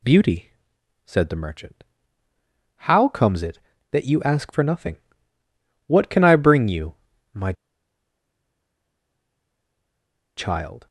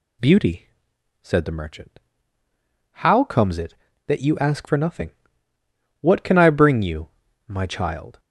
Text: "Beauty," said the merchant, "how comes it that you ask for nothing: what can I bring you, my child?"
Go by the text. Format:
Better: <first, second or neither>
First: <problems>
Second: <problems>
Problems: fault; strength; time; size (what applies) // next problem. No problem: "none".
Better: second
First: pauses between "my" and "child"; strong; at 7.5 s; 2.8 s long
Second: none